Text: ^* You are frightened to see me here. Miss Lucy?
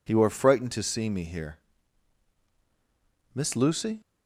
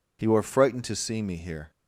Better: first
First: none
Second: stops before "Miss Lucy"; at 1.7 s

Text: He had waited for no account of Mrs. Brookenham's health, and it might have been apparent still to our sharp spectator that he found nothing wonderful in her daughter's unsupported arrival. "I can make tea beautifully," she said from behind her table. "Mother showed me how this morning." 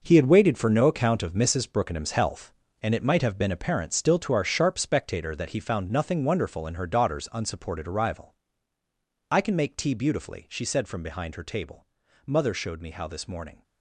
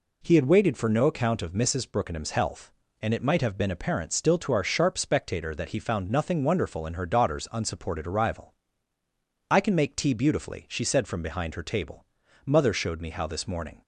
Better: second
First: gets quieter; strong; throughout; 10.5 dB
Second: none

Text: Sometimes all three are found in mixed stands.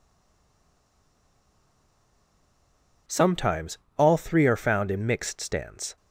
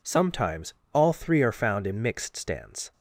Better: second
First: stays silent before the first word; strong; until 3.0 s; 3.0 s long // pauses between "Sometimes" and "all"; slight; at 3.7 s; 0.20 s long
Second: pauses between "Sometimes" and "all"; slight; at 0.7 s; 0.20 s long

